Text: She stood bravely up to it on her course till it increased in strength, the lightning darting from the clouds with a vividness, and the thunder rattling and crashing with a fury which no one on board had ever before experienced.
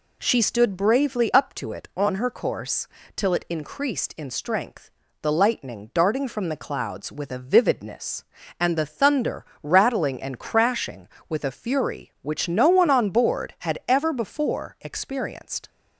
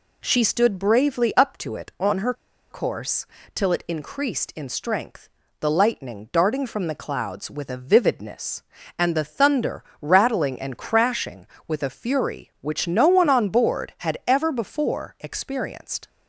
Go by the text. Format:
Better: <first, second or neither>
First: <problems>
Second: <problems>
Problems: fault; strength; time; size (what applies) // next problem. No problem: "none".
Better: first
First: pauses between "course" and "till"; slight; at 2.8 s; 0.26 s long // pauses between "thunder" and "rattling"; slight; at 9.4 s; 0.18 s long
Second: pauses between "her" and "course"; at 2.3 s; 0.38 s long // pauses between "course" and "till"; slight; at 3.2 s; 0.26 s long // pauses between "thunder" and "rattling"; slight; at 9.8 s; 0.18 s long